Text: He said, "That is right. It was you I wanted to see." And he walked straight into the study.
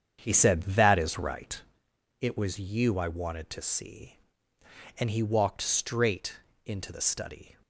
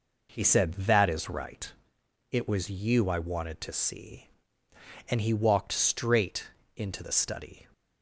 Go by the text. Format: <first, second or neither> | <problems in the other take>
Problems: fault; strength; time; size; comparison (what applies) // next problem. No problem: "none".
second | starts louder than the rest; strong; until 1.9 s; 8 dB // pauses between "straight" and "into"; slight; at 6.3 s; 0.30 s long; slight in the second